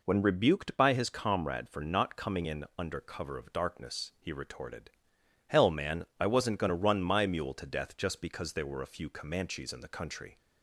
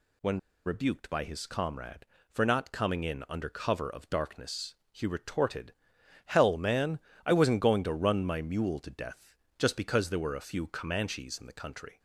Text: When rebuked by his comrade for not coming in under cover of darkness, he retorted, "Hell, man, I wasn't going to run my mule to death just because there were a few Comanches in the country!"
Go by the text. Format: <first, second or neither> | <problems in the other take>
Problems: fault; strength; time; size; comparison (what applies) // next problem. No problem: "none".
first | pauses between "When" and "rebuked"; slight; at 0.3 s; 0.26 s long // pauses between "death" and "just"; slight; at 9.3 s; 0.22 s long